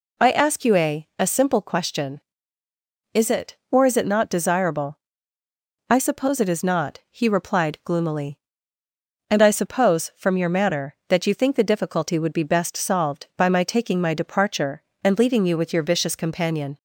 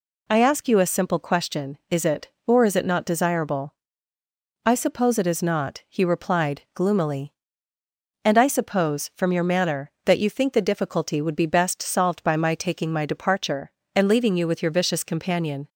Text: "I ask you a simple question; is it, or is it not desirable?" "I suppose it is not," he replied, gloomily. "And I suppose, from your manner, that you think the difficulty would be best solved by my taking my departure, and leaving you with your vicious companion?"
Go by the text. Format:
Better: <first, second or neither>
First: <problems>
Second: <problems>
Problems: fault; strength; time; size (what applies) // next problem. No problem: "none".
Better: second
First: says "a" twice; at 1.1 s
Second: none